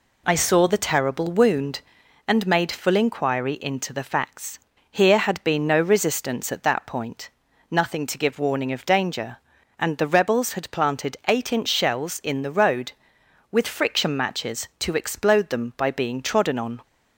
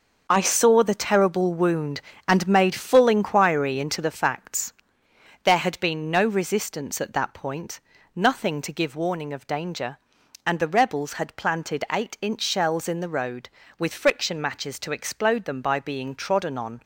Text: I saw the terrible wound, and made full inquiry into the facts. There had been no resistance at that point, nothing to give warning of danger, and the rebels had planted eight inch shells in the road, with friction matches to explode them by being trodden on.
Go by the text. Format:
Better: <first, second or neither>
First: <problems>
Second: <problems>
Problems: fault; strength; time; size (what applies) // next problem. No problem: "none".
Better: second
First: says "Here" for "There"; at 4.9 s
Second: none